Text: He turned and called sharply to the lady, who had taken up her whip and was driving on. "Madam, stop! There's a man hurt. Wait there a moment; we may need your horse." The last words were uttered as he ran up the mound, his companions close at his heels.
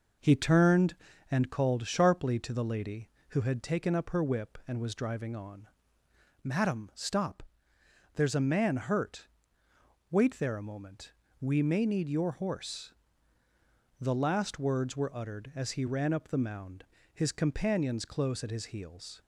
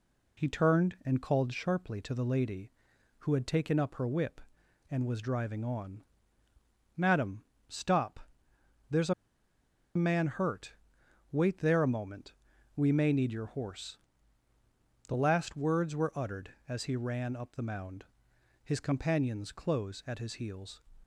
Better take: first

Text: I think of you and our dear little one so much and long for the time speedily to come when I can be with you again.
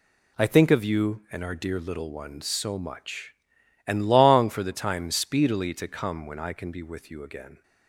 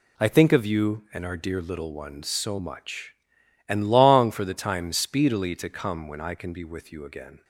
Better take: neither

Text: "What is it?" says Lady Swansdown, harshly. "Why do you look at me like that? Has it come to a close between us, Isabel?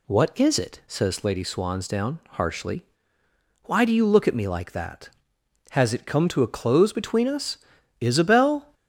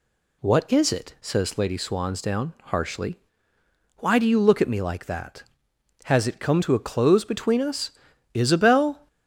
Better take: neither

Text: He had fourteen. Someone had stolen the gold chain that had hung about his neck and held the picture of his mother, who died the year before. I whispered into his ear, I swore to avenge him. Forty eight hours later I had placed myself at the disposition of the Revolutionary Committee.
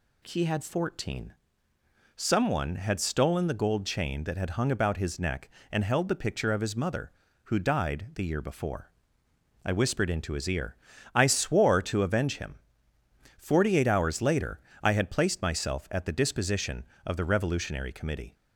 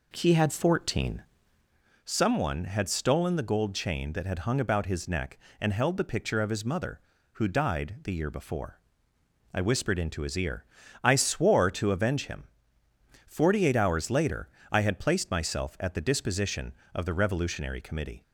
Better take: first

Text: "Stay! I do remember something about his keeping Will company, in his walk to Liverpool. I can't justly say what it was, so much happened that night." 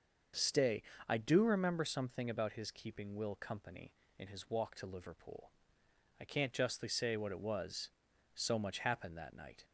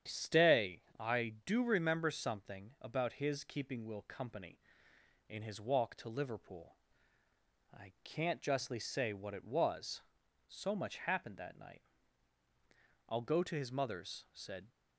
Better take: first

